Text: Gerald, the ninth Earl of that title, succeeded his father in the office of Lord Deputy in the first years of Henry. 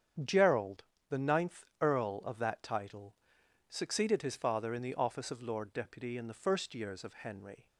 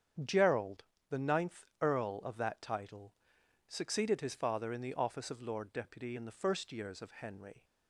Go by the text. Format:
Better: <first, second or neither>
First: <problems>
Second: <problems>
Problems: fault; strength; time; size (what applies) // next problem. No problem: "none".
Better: neither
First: starts louder than the rest; strong; until 1.5 s; 8 dB // pauses between "ninth" and "Earl"; slight; at 1.6 s; 0.16 s long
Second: starts louder than the rest; strong; until 1.5 s; 8 dB // pauses between "ninth" and "Earl"; slight; at 1.6 s; 0.16 s long